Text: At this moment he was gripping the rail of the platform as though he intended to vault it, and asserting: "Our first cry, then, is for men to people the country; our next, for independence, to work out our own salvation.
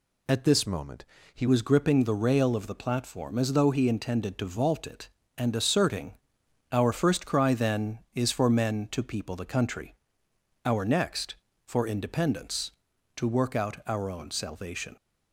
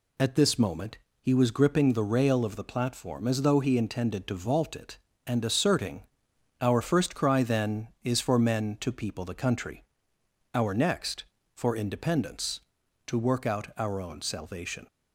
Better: second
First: changes voice from "moment" to "he"; from 0.6 to 1.4 s; 0.8 s long // pauses between "moment" and "he"; slight; at 1.0 s; 0.30 s long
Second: pauses between "moment" and "he"; slight; at 0.9 s; 0.24 s long

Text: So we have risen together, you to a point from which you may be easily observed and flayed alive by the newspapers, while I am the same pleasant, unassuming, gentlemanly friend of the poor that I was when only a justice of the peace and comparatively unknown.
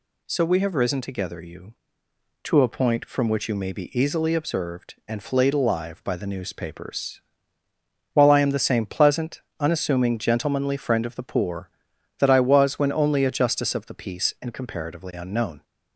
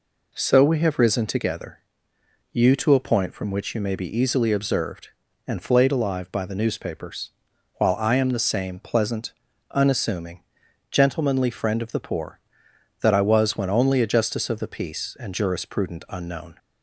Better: first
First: none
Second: says "jurisprudent" for "comparatively"; at 15.3 s

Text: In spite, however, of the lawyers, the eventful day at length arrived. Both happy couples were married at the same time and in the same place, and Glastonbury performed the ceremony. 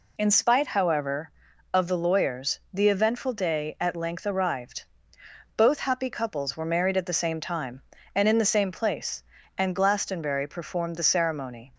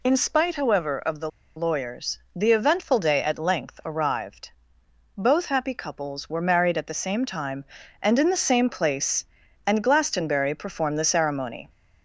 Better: first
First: none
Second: pauses between "the" and "lawyers"; slight; at 1.2 s; 0.27 s long

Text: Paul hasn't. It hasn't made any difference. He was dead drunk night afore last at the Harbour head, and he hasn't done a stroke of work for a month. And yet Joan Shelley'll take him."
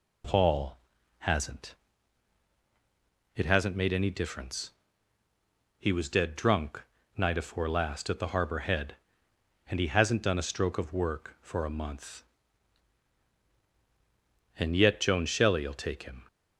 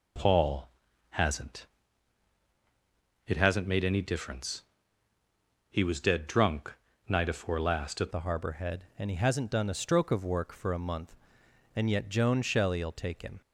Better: first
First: pauses between "Paul" and "hasn't"; at 0.7 s; 0.42 s long // pauses between "drunk" and "night"; slight; at 6.8 s; 0.36 s long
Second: pauses between "Paul" and "hasn't"; at 0.6 s; 0.42 s long // pauses between "drunk" and "night"; slight; at 6.7 s; 0.36 s long // changes voice at "the"; from 8.1 s on; 5.3 s long

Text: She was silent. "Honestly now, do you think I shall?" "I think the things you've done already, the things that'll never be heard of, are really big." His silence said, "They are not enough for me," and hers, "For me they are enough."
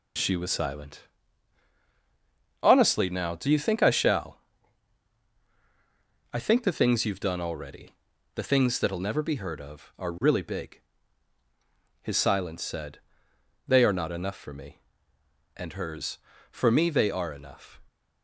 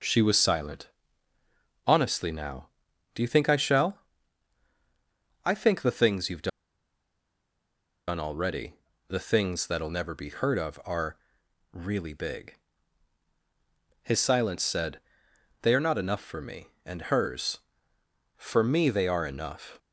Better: first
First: none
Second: pauses between "you've" and "done"; strong; at 6.4 s; 1.5 s long // pauses between "are" and "really"; noticeable; at 11.1 s; 0.56 s long

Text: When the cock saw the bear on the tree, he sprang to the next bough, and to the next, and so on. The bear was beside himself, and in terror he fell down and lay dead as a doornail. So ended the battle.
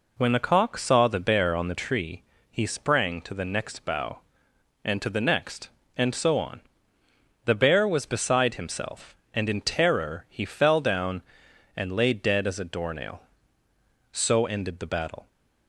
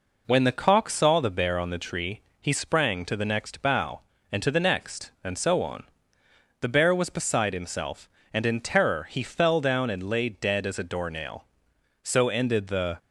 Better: first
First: none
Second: stops before "battle"; at 12.9 s

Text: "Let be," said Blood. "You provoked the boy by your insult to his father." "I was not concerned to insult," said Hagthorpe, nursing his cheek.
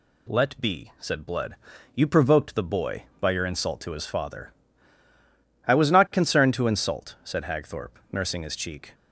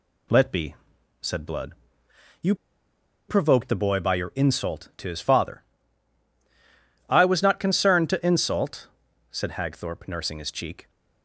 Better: first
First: none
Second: pauses between "You" and "provoked"; noticeable; at 2.5 s; 0.74 s long

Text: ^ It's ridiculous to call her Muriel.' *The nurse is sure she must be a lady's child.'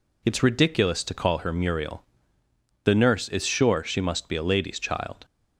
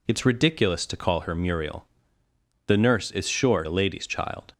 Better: first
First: none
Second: skips "she must be"; at 3.6 s

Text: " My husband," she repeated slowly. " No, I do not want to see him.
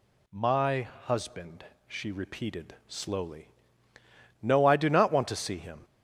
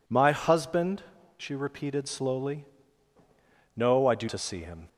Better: first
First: none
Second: skips "not want"; at 4.2 s

